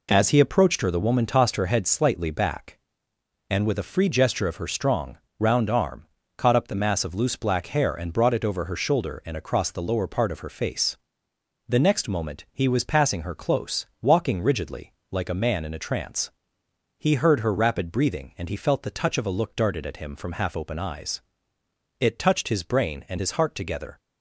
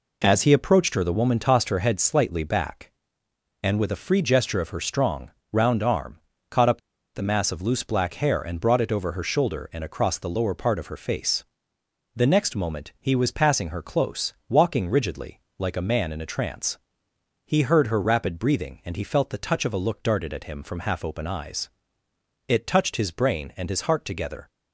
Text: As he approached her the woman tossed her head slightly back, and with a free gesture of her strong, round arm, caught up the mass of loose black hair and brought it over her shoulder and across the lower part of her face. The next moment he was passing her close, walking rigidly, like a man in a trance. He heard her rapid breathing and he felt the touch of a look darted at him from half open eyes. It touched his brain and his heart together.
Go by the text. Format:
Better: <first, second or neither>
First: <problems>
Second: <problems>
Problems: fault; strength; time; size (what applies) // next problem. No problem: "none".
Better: first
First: none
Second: pauses between "up" and "the"; slight; at 6.7 s; 0.35 s long